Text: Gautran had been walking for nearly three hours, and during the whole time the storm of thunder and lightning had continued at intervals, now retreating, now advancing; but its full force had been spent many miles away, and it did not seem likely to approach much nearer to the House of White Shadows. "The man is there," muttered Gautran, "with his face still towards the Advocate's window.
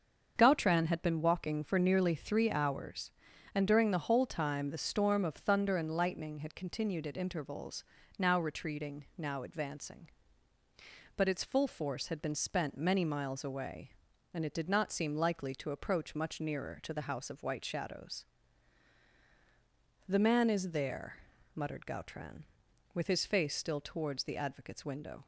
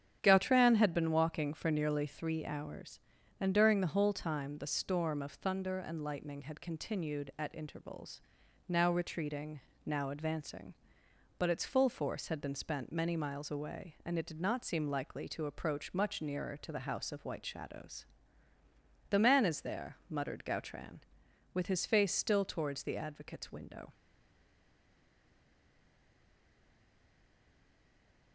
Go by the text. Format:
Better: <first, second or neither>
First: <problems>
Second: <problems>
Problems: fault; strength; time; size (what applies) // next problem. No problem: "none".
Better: first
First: starts louder than the rest; until 1.3 s; 7 dB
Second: starts louder than the rest; strong; until 1.2 s; 8.5 dB // stays silent after the last word; strong; from 23.9 s on; 4.4 s long